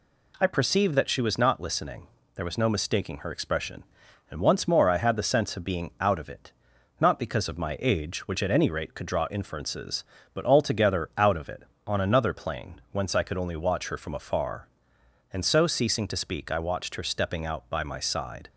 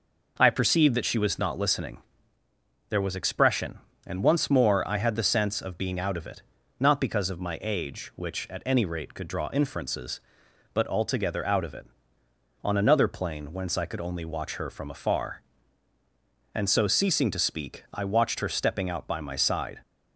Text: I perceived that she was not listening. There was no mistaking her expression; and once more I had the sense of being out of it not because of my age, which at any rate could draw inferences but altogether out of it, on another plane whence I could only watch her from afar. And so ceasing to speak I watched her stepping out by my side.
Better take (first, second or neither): first